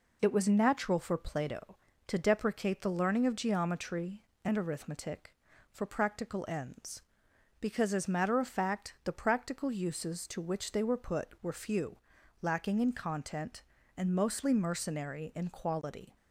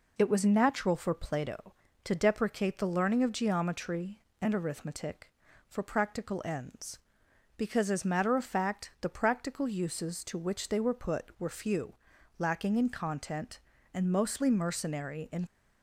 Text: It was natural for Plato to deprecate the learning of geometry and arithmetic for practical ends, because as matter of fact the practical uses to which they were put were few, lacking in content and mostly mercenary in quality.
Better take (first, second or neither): first